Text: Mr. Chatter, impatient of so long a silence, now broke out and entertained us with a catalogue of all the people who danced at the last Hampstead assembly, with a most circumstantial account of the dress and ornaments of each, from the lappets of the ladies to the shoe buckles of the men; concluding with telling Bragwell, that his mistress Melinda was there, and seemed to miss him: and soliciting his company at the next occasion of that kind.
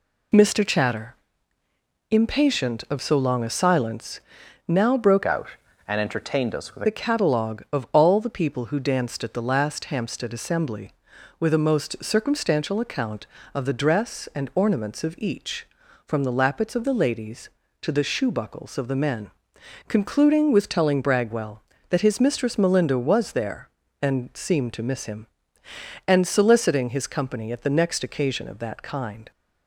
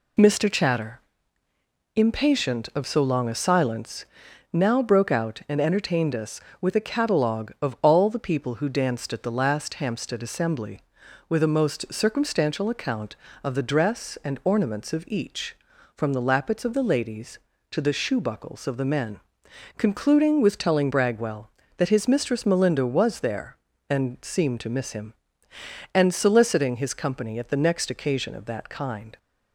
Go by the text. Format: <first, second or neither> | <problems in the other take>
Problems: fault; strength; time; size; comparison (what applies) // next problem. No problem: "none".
second | changes voice from "out" to "with"; from 5.2 to 6.8 s; 1.6 s long